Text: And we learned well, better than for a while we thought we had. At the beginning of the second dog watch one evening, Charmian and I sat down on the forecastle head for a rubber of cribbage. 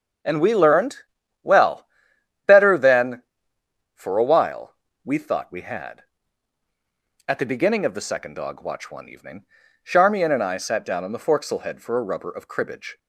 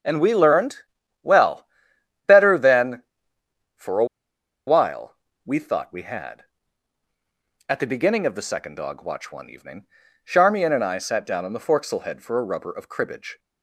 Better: first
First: starts louder than the rest; strong; until 1.7 s; 7 dB // pauses between "learned" and "well"; noticeable; at 0.9 s; 0.46 s long // pauses between "while" and "we"; slight; at 4.7 s; 0.30 s long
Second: starts louder than the rest; strong; until 1.4 s; 7 dB // pauses between "learned" and "well"; noticeable; at 0.7 s; 0.46 s long // pauses between "a" and "while"; noticeable; at 4.0 s; 0.62 s long // pauses between "while" and "we"; slight; at 5.1 s; 0.30 s long

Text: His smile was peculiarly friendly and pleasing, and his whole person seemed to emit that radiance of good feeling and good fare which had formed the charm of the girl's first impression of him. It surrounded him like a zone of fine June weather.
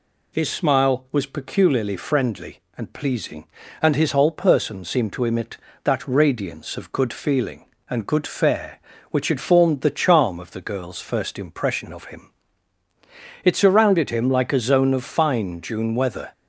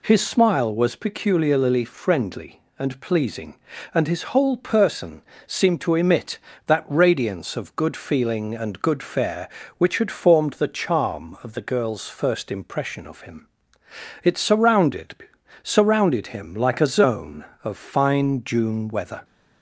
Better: first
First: none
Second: pauses between "person" and "seemed"; slight; at 5.2 s; 0.24 s long // says "surrounded" twice; at 15.6 s

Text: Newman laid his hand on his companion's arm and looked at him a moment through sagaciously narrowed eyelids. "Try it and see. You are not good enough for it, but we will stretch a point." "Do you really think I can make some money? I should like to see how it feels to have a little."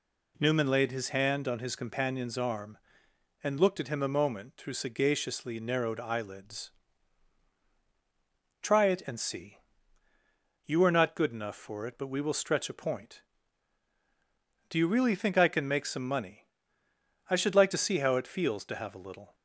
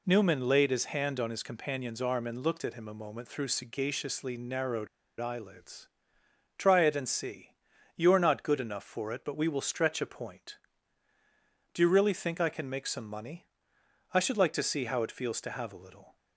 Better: first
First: none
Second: pauses between "narrowed" and "eyelids"; slight; at 4.8 s; 0.32 s long

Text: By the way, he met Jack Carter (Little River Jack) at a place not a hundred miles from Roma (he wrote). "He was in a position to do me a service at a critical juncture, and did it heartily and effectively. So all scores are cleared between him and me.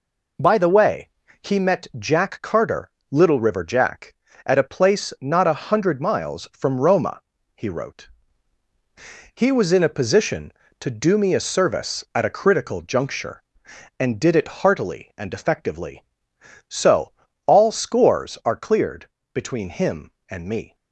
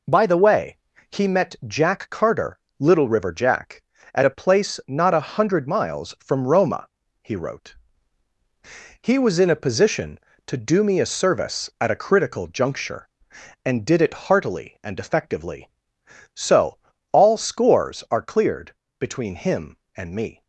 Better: neither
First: pauses between "So" and "all"; slight; at 17.1 s; 0.32 s long // pauses between "cleared" and "between"; slight; at 19.0 s; 0.24 s long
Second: pauses between "So" and "all"; slight; at 16.7 s; 0.32 s long // pauses between "cleared" and "between"; slight; at 18.7 s; 0.24 s long

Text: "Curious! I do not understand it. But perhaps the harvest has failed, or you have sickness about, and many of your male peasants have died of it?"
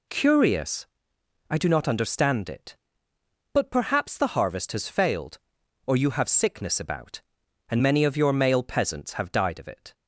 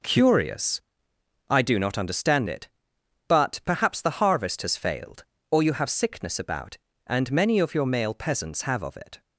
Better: first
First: none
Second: skips "died"; at 8.8 s

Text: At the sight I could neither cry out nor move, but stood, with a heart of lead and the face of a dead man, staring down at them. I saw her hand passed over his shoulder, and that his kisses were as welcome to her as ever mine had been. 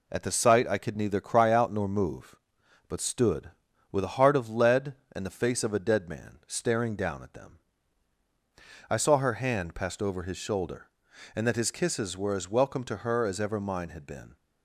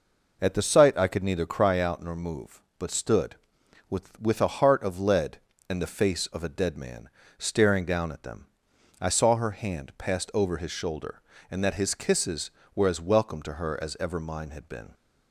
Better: first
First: none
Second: says "with" twice; at 4.2 s

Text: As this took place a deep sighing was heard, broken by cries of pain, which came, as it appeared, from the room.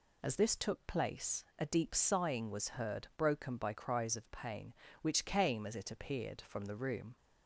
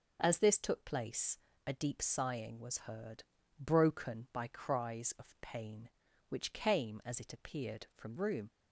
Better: first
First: none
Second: pauses between "place" and "a"; slight; at 1.3 s; 0.26 s long // skips "the"; at 8.1 s

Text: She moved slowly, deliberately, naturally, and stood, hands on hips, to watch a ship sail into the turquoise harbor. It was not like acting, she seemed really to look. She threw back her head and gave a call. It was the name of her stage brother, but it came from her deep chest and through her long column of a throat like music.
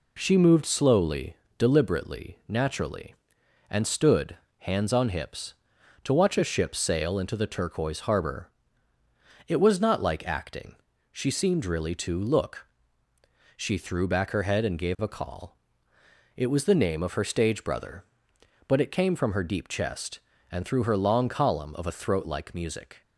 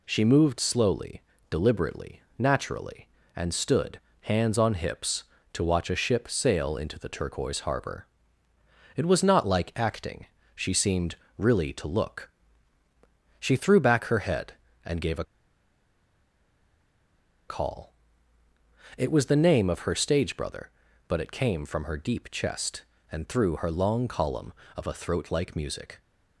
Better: first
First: none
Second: pauses between "seemed" and "really"; slight; at 11.1 s; 0.22 s long // pauses between "a" and "call"; strong; at 15.2 s; 2.2 s long

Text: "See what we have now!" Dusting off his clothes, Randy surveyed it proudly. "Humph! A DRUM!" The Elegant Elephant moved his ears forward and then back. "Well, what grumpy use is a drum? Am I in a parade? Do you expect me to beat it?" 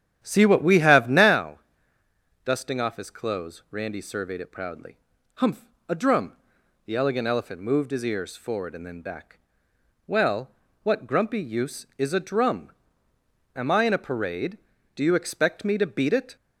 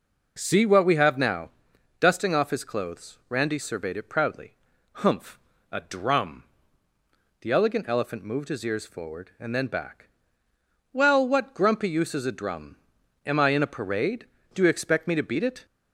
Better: second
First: starts louder than the rest; strong; until 1.4 s; 10 dB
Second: none

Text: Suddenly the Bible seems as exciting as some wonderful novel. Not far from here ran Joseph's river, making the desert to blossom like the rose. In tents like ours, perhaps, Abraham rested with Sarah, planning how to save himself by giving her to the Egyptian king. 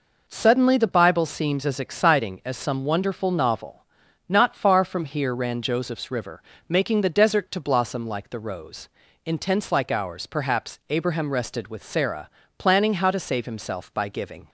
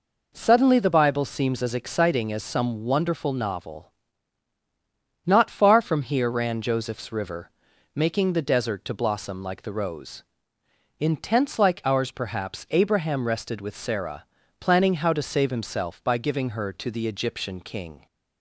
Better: second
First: stops before "her to the Egyptian king"; at 14.4 s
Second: none

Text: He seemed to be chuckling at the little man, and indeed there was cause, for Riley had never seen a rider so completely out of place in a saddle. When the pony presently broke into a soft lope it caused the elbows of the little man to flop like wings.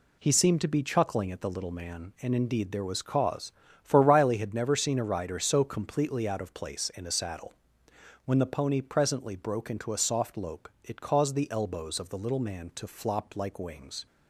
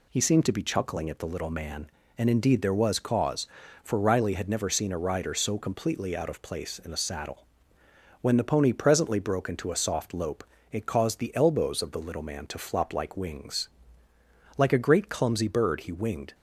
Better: first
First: pauses between "lope" and "it"; slight; at 10.6 s; 0.16 s long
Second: pauses between "lope" and "it"; slight; at 10.4 s; 0.26 s long // goes on to say "Like a great clumsy bird he winged"; strong; from 14.5 s on; 1.7 s long

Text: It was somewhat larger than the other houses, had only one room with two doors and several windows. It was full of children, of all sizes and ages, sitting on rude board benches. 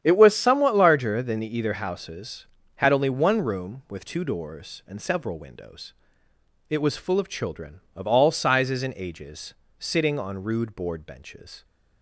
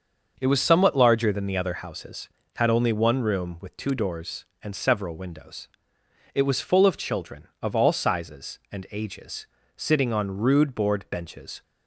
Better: second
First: starts louder than the rest; strong; until 1.0 s; 9.5 dB // says "either" for "other"; at 1.5 s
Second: starts louder than the rest; noticeable; until 1.3 s; 6 dB

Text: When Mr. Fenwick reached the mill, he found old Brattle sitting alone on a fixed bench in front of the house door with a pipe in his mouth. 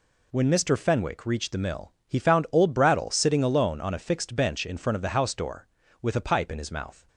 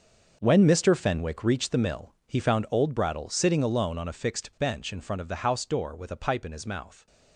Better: first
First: none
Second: gets quieter; strong; throughout; 12.5 dB

